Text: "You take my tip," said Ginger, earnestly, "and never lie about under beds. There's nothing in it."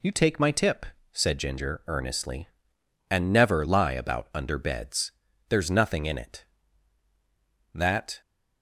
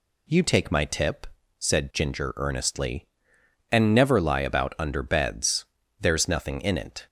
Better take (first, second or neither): second